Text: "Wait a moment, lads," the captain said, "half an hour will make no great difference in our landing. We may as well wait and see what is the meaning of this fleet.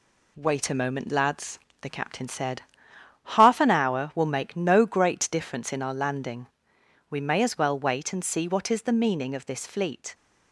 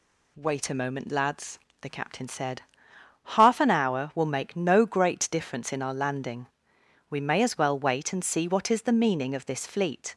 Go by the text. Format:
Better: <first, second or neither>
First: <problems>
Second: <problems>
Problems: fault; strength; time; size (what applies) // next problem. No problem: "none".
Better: second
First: gets quieter; throughout; 3.5 dB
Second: none